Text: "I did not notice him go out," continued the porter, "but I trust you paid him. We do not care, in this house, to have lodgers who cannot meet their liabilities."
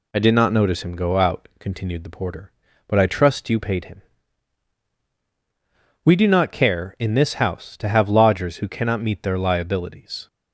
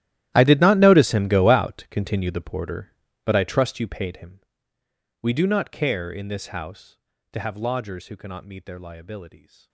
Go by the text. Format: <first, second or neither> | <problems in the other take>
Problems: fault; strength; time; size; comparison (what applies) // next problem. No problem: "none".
first | gets quieter; strong; throughout; 19.5 dB